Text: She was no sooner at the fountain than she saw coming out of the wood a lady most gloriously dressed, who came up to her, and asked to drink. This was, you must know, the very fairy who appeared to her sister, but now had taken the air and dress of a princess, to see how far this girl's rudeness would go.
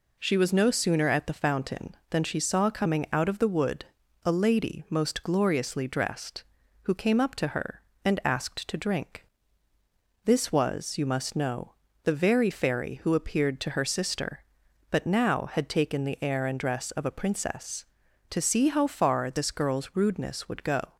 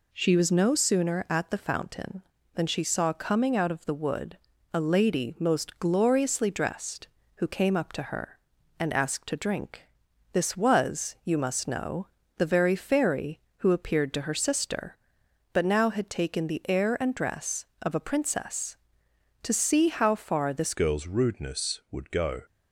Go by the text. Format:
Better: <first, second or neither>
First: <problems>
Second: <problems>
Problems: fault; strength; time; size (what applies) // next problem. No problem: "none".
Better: first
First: pauses between "wood" and "a"; at 3.8 s; 0.40 s long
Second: pauses between "wood" and "a"; slight; at 4.3 s; 0.36 s long // changes voice at "girl's"; from 20.7 s on; 1.7 s long